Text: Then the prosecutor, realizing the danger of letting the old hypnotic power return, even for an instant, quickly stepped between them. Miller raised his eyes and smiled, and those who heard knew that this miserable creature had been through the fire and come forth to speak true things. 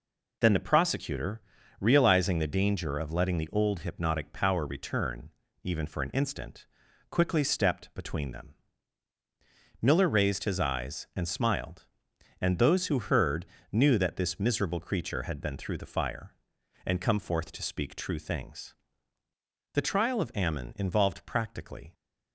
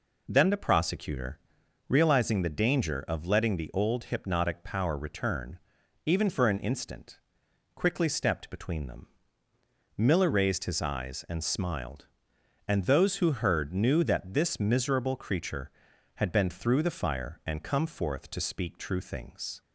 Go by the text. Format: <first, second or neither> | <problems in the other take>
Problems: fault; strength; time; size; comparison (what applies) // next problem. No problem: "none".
second | pauses between "heard" and "knew"; slight; at 13.4 s; 0.26 s long // goes on to say "The trial of Ammon involved practically"; strong; from 19.7 s on; 2.2 s long